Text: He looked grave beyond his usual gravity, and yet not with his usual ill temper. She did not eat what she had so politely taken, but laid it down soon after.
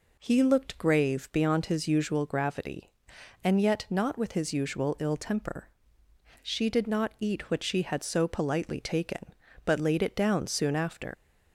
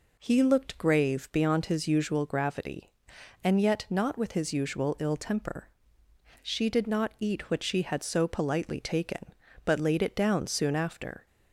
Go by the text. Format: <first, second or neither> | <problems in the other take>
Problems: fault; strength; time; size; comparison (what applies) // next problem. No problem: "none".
second | leaves "after" unfinished; at 11.1 s; 110 ms